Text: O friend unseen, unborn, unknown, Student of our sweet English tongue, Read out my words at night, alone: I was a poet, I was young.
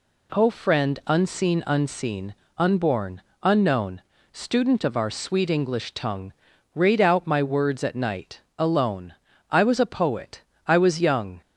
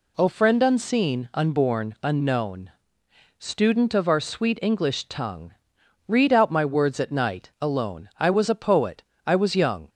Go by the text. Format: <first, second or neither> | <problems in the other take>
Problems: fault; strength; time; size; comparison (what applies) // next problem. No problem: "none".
second | says "unseen" twice; at 1.6 s